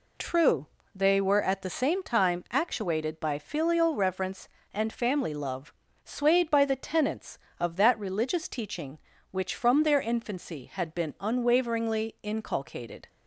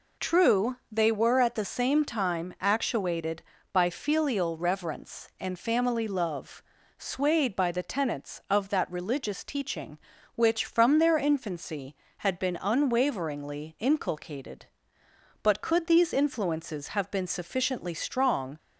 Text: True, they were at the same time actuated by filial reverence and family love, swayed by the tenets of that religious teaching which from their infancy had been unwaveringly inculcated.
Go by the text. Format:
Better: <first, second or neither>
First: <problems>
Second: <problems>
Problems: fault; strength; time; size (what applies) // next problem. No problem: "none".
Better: first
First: none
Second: goes on to say "But could these influences have been sufficiently strong"; strong; from 15.4 s on; 3.1 s long